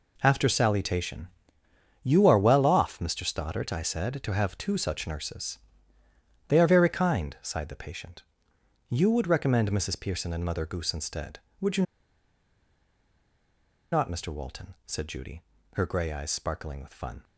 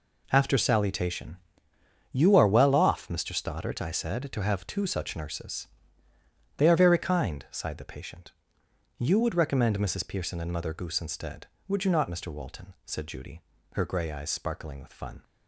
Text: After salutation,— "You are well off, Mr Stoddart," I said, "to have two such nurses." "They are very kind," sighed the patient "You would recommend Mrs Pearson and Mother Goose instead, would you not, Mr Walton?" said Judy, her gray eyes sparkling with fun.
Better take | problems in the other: second | pauses between "patient" and "You"; noticeable; at 8.2 s; 0.66 s long; noticeable in the second // pauses between "you" and "not"; strong; at 11.8 s; 2.0 s long

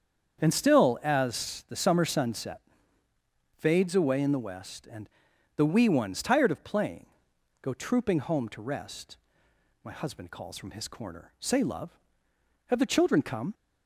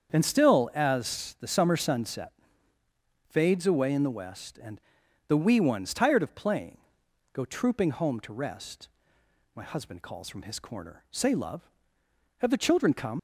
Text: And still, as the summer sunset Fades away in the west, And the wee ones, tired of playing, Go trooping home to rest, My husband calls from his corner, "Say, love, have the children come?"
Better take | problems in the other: first | starts louder than the rest; strong; until 1.1 s; 7.5 dB; strong in the first // pauses between "sunset" and "Fades"; noticeable; at 2.3 s; 0.96 s long; noticeable in the first // pauses between "And" and "the"; noticeable; at 4.8 s; 0.46 s long; noticeable in the first // leaves "come" unfinished; at 13.1 s; 50 ms

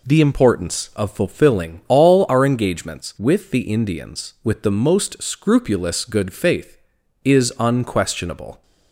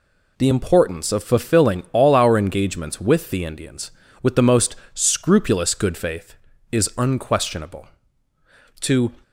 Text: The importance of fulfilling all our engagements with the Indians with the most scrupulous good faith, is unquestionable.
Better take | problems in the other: first | pauses between "most" and "scrupulous"; slight; at 4.7 s; 0.20 s long // goes on to say "To"; slight; from 8.8 s on; 0.32 s long

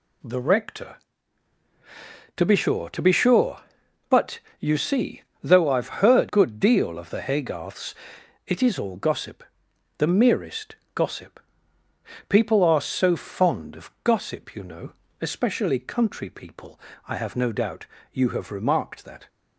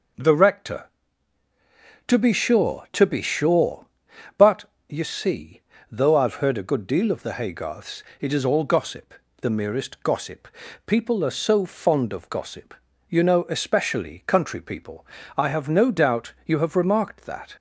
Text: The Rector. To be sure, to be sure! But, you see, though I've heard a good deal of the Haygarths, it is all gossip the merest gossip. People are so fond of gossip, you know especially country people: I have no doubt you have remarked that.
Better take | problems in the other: second | skips "a"; at 6.2 s // pauses between "gossip" and "the"; noticeable; at 9.4 s; 0.54 s long; slight in the second // pauses between "merest" and "gossip"; slight; at 10.7 s; 0.18 s long // pauses between "know" and "especially"; slight; at 14.9 s; 0.30 s long // pauses between "doubt" and "you"; slight; at 17.8 s; 0.28 s long

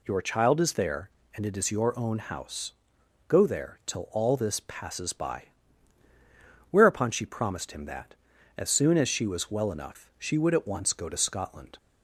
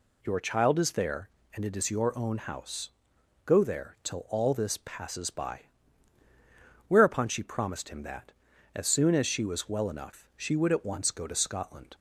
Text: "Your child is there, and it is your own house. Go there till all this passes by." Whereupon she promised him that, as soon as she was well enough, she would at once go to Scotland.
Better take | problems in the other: neither | none

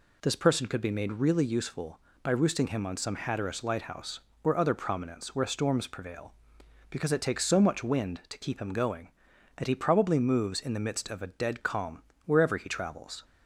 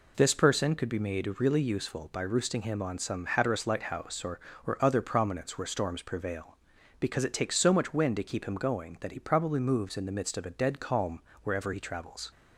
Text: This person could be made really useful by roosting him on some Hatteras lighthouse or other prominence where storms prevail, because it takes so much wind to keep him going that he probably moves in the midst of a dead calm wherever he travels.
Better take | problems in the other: first | says "or" twice; at 4.6 s // pauses between "calm" and "wherever"; slight; at 11.2 s; 0.22 s long; slight in the first

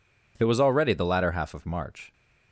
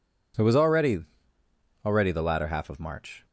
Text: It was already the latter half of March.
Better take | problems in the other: first | says "already" twice; at 1.8 s

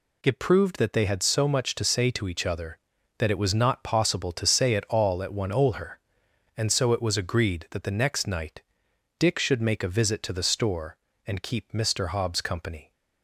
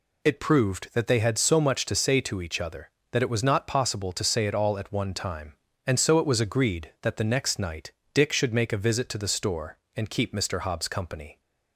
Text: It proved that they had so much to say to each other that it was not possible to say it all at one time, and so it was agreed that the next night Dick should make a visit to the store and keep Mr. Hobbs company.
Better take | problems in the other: second | says "olher" for "time"; at 5.5 s // pauses between "night" and "Dick"; noticeable; at 8.6 s; 0.56 s long; slight in the second

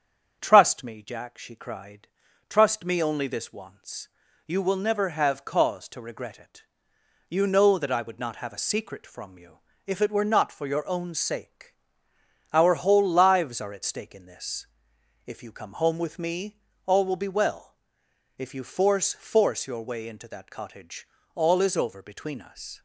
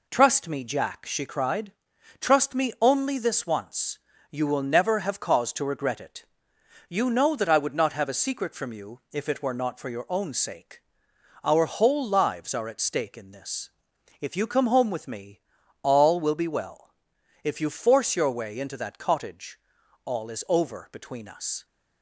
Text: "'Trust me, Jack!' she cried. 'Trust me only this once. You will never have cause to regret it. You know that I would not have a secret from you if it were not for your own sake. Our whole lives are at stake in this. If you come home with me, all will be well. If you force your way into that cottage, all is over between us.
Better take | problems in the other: second | starts louder than the rest; strong; until 1.4 s; 7.5 dB // pauses between "you" and "if"; slight; at 9.5 s; 0.28 s long // says "force" twice; at 19.1 s

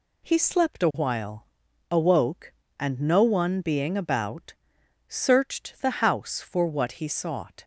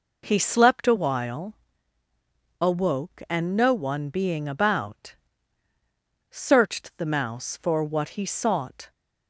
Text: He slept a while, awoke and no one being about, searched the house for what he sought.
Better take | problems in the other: first | says "mouse" for "house"; at 7.0 s

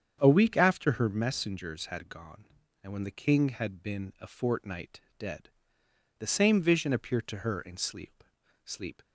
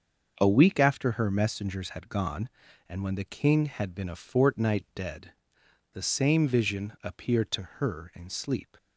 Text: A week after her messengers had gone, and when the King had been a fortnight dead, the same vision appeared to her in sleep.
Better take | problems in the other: second | starts louder than the rest; strong; until 1.2 s; 7.5 dB; also in the second // pauses between "fortnight" and "dead"; slight; at 4.9 s; 0.18 s long // says "sleep" twice; at 8.6 s

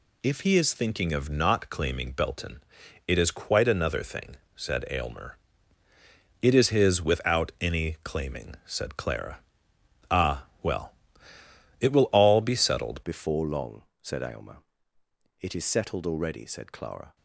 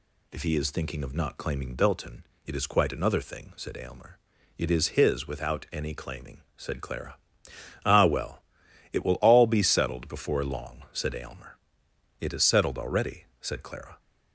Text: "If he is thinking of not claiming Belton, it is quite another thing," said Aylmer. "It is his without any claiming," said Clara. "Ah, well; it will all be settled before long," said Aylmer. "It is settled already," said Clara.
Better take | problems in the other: second | changes voice at "before"; from 13.0 s on; 4.1 s long

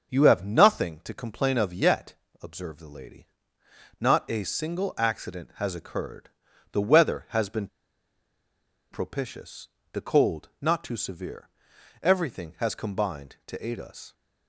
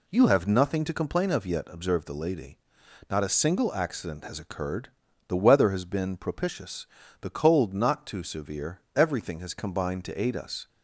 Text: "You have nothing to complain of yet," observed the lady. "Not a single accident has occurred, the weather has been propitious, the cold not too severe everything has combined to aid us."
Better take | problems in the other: second | starts louder than the rest; until 1.1 s; 6.5 dB // pauses between "been" and "propitious"; strong; at 7.6 s; 1.2 s long // pauses between "severe" and "everything"; noticeable; at 11.4 s; 0.54 s long

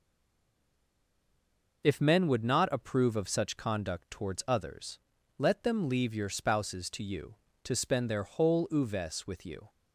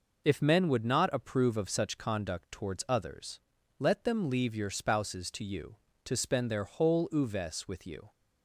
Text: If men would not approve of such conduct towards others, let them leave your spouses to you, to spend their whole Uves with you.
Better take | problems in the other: second | stays silent before the first word; noticeable; until 1.8 s; 1.8 s long

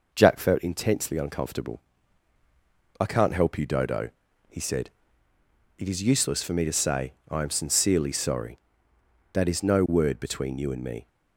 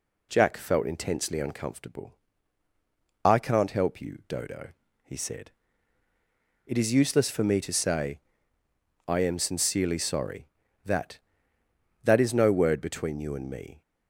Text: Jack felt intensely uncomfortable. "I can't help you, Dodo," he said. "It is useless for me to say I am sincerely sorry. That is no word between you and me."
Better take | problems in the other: first | pauses between "say" and "I"; noticeable; at 8.1 s; 0.87 s long; slight in the first // says "That" twice; at 12.0 s

